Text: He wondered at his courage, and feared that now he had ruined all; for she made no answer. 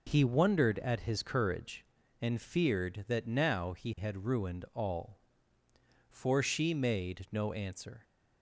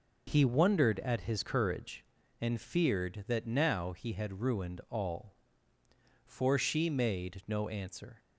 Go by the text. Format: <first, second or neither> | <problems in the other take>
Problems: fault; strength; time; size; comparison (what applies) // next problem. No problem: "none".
neither | none